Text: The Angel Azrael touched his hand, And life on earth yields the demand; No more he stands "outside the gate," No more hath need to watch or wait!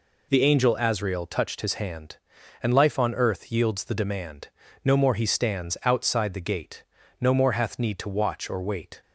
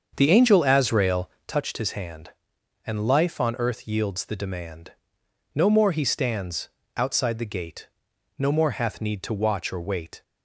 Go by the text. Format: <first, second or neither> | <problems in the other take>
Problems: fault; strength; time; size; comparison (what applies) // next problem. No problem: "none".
first | starts louder than the rest; until 1.6 s; 7 dB // pauses between "Azrael" and "touched"; slight; at 1.2 s; 0.20 s long // pauses between "stands" and "outside"; slight; at 6.6 s; 0.28 s long